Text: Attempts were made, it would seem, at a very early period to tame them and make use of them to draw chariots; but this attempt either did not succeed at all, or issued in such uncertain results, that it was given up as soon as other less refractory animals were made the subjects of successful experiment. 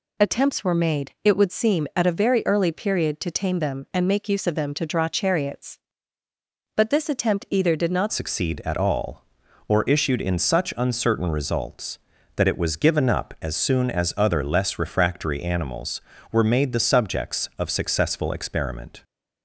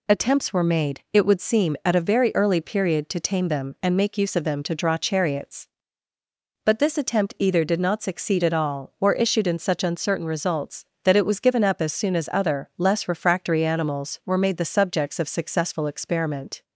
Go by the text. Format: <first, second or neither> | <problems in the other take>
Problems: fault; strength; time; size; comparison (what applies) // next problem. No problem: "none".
second | changes voice at "succeed"; from 8.1 s on; 10.9 s long